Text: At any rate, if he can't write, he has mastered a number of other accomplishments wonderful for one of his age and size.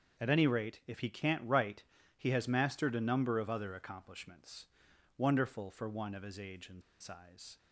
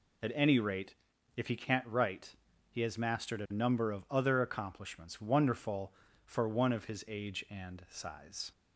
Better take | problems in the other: second | starts louder than the rest; until 1.2 s; 6.5 dB // pauses between "accomplishments" and "wonderful"; noticeable; at 4.6 s; 0.52 s long // pauses between "and" and "size"; slight; at 6.8 s; 0.19 s long

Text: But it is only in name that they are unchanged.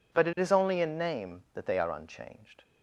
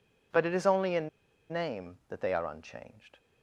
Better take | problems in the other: first | pauses between "in" and "name"; at 1.0 s; 0.42 s long

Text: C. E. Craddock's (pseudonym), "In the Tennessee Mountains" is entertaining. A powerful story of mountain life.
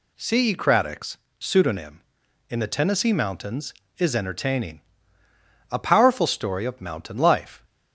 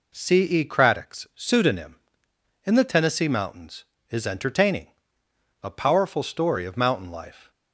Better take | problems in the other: neither | none

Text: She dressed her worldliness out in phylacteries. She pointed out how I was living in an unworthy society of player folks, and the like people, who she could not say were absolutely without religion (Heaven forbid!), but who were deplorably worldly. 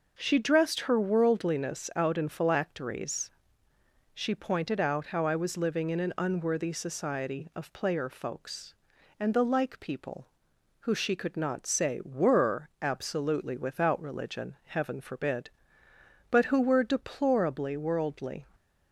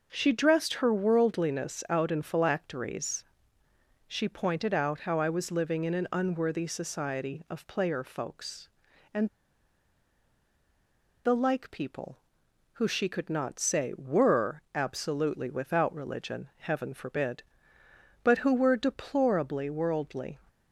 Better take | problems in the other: first | pauses between "and" and "the"; strong; at 9.2 s; 1.9 s long

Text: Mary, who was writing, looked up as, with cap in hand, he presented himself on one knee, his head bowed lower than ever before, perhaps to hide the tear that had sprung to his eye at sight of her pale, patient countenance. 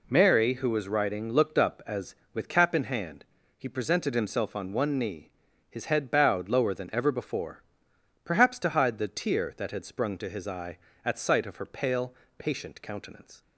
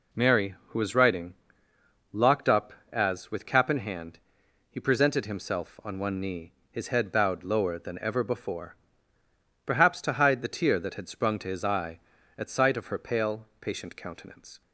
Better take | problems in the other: first | says "locked" for "looked"; at 2.1 s

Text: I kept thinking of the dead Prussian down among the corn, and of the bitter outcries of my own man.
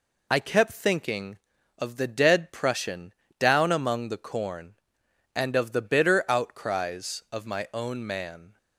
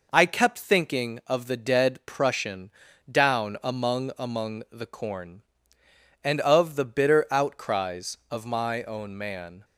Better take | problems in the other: first | pauses between "Prussian" and "down"; at 2.7 s; 0.40 s long; slight in the first // says "among" twice; at 4.1 s

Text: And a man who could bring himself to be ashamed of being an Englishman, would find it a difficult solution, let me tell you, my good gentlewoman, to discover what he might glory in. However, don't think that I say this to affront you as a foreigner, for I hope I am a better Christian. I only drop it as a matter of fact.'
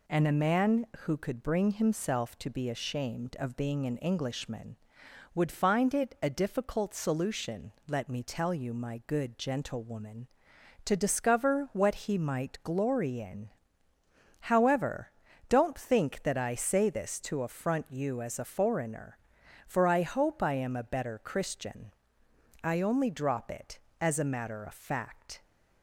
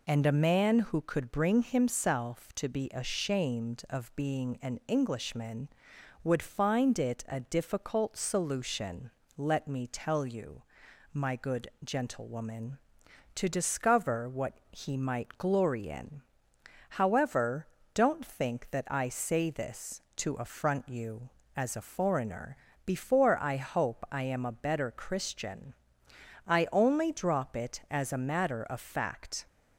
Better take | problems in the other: first | pauses between "good" and "gentlewoman"; slight; at 11.6 s; 0.16 s long // pauses between "what" and "he"; slight; at 14.5 s; 0.18 s long // says "before" for "for"; at 22.8 s

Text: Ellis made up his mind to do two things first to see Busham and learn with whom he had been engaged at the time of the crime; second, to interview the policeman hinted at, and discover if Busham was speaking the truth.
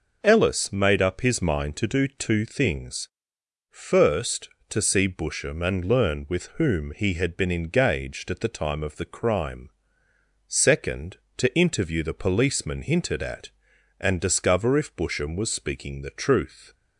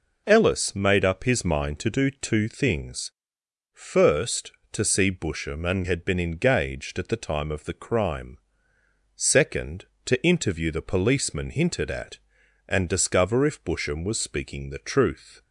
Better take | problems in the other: first | pauses between "things" and "first"; noticeable; at 3.0 s; 0.62 s long; noticeable in the first // skips "learn with whom he"; at 5.8 s

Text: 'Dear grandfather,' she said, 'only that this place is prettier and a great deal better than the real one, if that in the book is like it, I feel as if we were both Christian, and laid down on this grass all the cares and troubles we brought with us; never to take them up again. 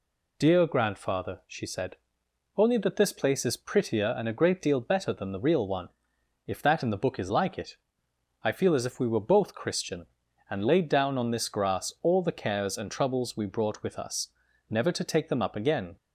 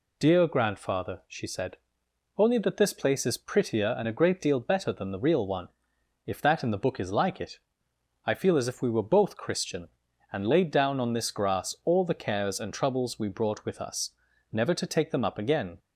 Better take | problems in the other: neither | none

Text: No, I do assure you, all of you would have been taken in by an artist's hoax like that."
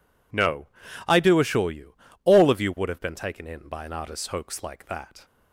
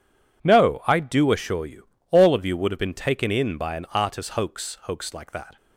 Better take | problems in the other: first | says "hoax" twice; at 4.8 s

